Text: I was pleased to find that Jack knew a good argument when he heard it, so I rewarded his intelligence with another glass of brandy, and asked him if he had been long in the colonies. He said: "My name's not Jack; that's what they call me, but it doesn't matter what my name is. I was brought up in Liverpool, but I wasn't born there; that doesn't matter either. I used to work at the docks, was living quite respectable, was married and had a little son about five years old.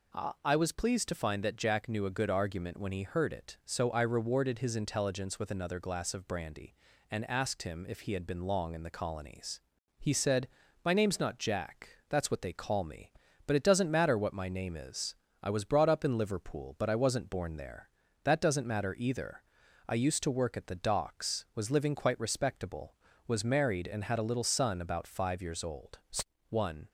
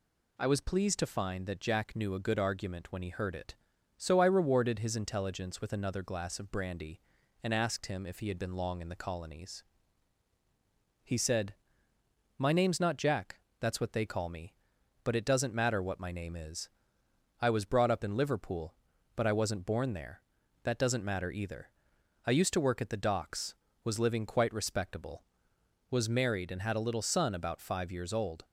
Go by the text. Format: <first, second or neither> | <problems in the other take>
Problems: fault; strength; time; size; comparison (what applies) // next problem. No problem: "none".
second | goes on to say "One"; slight; from 26.4 s on; 0.40 s long